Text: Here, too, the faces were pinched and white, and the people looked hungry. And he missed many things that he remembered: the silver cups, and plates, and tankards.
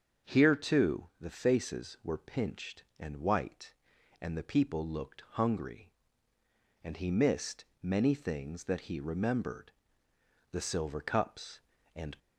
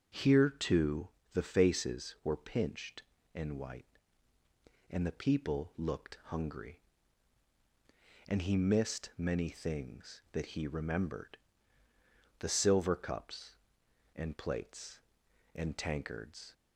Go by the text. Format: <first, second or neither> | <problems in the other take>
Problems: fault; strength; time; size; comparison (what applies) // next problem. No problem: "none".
second | starts louder than the rest; until 1.3 s; 7 dB; also in the second // pauses between "missed" and "many"; slight; at 7.6 s; 0.18 s long // stops before "plates and tankards"; at 12.1 s